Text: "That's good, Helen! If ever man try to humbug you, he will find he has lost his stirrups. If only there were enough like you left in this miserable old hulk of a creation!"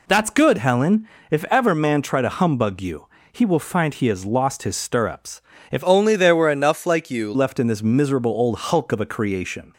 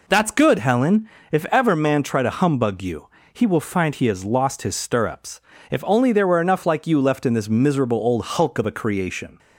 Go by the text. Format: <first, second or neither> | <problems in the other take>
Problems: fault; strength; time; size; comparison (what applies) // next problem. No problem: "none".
second | changes voice from "only" to "you"; from 5.8 to 7.2 s; 1.4 s long